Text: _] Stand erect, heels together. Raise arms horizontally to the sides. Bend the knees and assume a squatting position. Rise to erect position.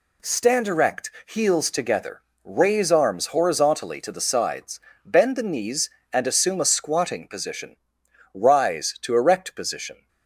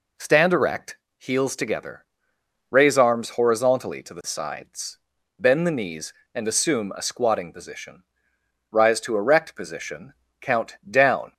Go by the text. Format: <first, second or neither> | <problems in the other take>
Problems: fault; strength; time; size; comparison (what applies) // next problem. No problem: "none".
first | goes on to say "Count down"; noticeable; from 10.4 s on; 0.92 s long